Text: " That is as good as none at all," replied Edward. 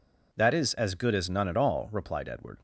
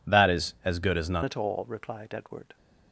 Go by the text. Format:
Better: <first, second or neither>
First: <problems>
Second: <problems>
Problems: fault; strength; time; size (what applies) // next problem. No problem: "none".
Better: first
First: none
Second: changes voice at "at"; from 1.2 s on; 1.3 s long